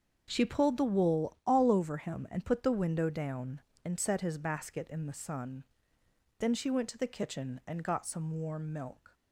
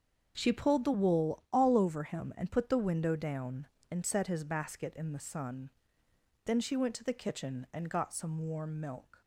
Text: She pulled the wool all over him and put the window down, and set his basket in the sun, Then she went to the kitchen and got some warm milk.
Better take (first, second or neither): neither